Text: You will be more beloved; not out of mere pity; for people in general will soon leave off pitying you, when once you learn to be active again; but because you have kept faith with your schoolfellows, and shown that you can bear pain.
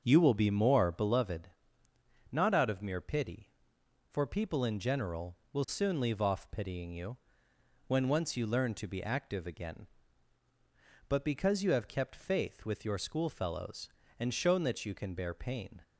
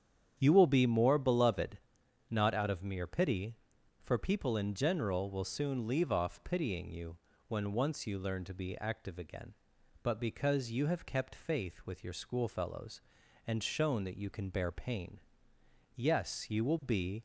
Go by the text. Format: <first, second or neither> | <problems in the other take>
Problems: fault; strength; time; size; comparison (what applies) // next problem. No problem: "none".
first | starts louder than the rest; strong; until 1.3 s; 8.5 dB; also in the first // goes on to say "Yes you will be"; noticeable; from 15.9 s on; 1.2 s long